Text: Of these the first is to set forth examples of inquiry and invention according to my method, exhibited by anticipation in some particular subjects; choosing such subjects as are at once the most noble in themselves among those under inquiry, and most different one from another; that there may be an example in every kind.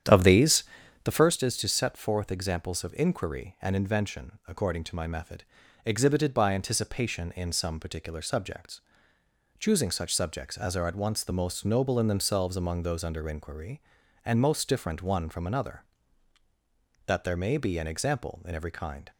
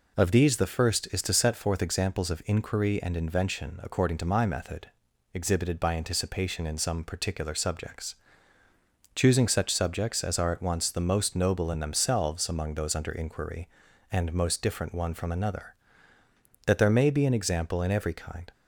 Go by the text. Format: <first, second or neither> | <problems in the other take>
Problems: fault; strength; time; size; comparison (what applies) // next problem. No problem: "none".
second | starts louder than the rest; strong; until 1.3 s; 9.5 dB // pauses between "these" and "the"; at 0.6 s; 0.40 s long